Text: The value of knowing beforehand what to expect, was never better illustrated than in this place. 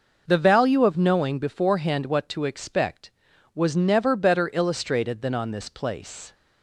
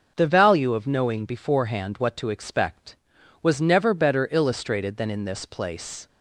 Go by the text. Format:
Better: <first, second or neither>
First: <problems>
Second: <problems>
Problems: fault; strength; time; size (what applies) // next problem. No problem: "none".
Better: second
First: says "on" for "in"; at 5.3 s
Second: none